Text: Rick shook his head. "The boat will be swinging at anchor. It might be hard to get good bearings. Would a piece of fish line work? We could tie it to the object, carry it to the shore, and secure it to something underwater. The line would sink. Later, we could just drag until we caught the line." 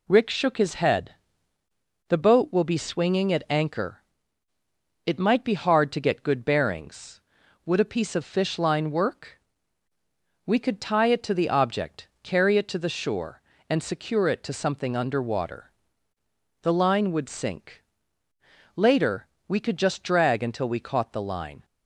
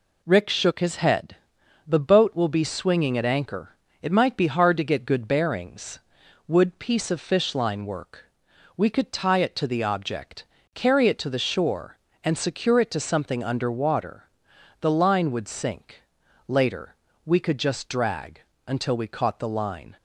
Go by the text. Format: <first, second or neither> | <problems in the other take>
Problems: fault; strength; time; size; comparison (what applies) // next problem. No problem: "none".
first | skips "a"; at 6.7 s // pauses between "drag" and "until"; slight; at 18.4 s; 0.22 s long